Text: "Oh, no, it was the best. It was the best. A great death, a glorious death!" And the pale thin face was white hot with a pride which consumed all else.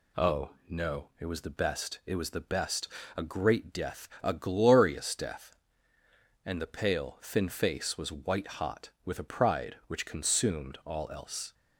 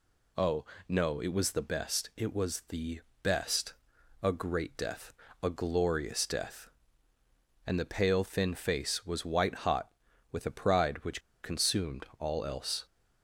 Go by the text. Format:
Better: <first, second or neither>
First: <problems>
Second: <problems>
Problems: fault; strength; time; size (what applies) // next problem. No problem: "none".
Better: first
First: none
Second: pauses between "the" and "best"; slight; at 3.0 s; 0.20 s long // pauses between "which" and "consumed"; slight; at 11.2 s; 0.22 s long